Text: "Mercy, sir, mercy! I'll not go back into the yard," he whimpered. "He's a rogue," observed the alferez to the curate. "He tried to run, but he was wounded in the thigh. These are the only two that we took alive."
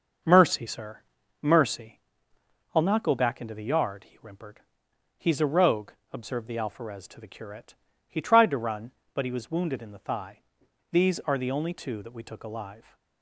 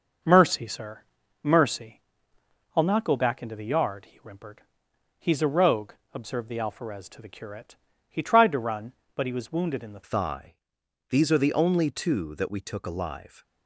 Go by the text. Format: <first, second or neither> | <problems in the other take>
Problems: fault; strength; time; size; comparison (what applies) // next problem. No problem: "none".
first | starts louder than the rest; noticeable; until 1.6 s; 6 dB; noticeable in the first // changes voice at "thigh"; from 10.0 s on; 3.4 s long